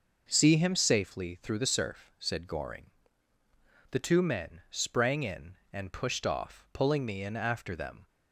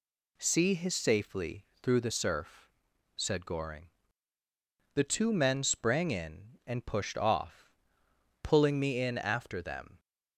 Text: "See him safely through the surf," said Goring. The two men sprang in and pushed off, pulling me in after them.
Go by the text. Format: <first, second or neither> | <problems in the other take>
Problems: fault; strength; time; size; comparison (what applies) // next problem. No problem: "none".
first | says "his" for "him"; at 0.7 s // pauses between "safely" and "through"; slight; at 1.6 s; 0.18 s long